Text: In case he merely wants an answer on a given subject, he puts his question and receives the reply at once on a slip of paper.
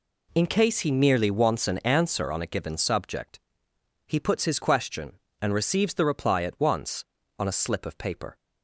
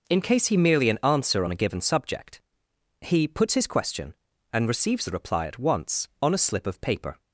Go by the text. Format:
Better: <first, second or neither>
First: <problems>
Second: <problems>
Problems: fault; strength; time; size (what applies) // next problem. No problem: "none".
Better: first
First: none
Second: skips "wants"; at 0.8 s